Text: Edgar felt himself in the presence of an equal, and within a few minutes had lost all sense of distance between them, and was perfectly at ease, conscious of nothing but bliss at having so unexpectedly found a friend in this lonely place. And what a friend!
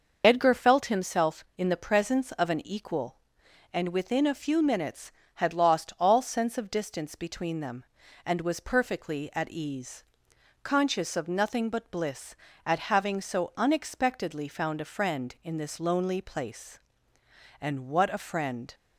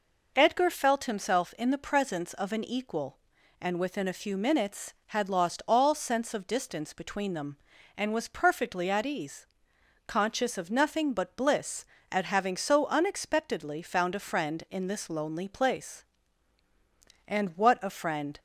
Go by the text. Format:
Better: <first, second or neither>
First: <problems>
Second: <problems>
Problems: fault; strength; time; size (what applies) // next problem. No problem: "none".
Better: second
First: loses the start of "Edgar"; at 0.2 s; 45 ms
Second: none